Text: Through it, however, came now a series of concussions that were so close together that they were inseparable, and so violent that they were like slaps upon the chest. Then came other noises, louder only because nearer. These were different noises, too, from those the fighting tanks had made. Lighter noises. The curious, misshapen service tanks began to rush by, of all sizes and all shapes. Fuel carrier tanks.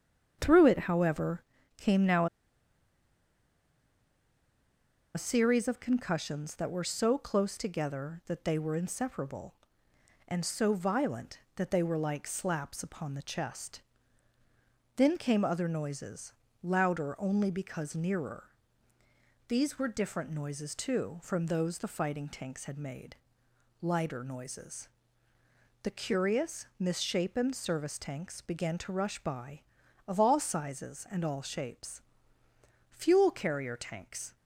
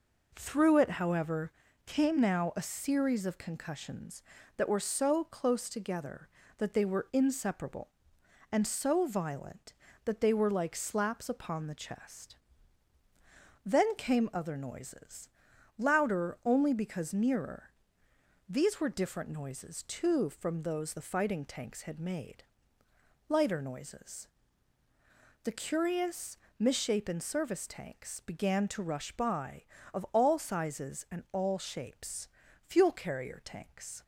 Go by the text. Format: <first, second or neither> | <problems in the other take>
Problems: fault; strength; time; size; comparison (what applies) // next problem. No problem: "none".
second | starts louder than the rest; strong; until 1.4 s; 7.5 dB // pauses between "now" and "a"; strong; at 2.2 s; 2.8 s long